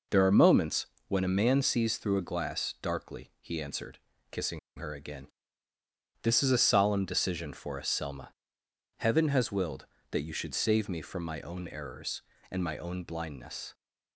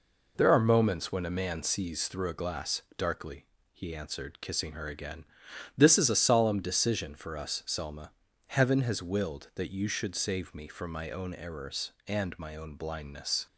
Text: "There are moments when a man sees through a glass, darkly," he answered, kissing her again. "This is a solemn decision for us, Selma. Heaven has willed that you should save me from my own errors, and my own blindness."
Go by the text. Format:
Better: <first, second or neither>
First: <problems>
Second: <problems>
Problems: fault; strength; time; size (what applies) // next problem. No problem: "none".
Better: second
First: pauses between "moments" and "when"; slight; at 0.8 s; 0.22 s long // pauses between "kissing" and "her"; slight; at 4.5 s; 0.18 s long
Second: none